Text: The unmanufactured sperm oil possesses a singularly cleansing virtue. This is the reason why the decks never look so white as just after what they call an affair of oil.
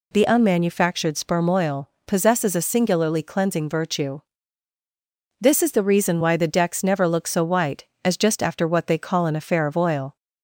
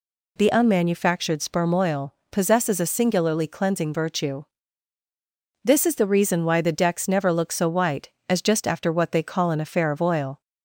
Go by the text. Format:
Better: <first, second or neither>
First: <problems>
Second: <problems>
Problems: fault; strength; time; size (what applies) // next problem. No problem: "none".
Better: neither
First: pauses between "oil" and "possesses"; slight; at 1.8 s; 0.16 s long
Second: pauses between "oil" and "possesses"; slight; at 2.1 s; 0.16 s long